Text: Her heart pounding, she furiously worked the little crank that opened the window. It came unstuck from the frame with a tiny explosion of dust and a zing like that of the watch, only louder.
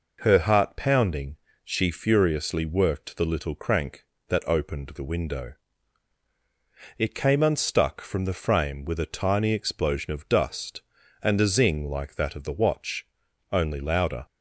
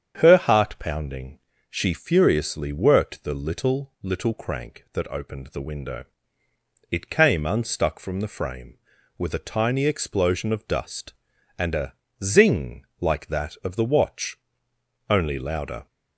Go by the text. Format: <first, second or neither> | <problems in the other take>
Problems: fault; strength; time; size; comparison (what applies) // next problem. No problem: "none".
first | starts louder than the rest; strong; until 1.2 s; 8 dB // says "little" twice; at 4.0 s // pauses between "a" and "zing"; slight; at 11.9 s; 0.32 s long